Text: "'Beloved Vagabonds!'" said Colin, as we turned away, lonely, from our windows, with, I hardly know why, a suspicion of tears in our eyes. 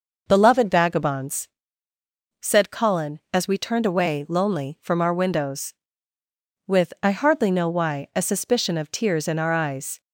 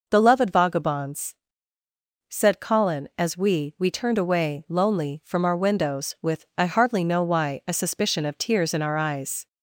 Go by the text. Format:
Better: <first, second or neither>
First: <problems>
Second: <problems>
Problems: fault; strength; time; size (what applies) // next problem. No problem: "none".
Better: first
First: none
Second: says "we" twice; at 3.7 s